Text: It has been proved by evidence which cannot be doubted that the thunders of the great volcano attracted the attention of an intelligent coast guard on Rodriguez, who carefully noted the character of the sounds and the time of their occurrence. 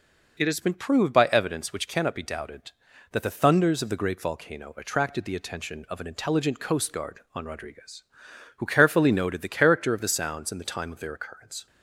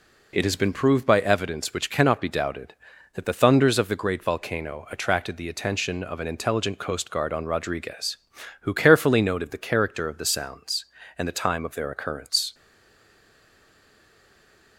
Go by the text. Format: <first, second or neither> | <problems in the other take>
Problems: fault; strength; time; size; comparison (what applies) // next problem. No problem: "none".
first | stays silent after the last word; from 12.5 s on; 2.2 s long